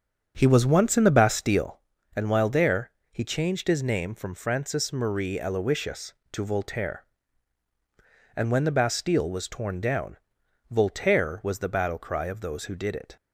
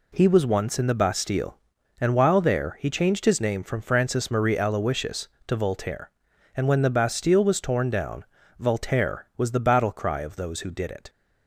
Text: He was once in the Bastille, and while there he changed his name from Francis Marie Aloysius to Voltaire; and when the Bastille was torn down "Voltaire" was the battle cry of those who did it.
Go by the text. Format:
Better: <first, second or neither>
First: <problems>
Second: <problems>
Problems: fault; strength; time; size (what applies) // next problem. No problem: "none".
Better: second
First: starts louder than the rest; strong; until 1.8 s; 7.5 dB // pauses between "there" and "he"; slight; at 2.8 s; 0.20 s long // pauses between "down" and "Voltaire"; noticeable; at 10.1 s; 0.52 s long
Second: pauses between "down" and "Voltaire"; slight; at 8.2 s; 0.36 s long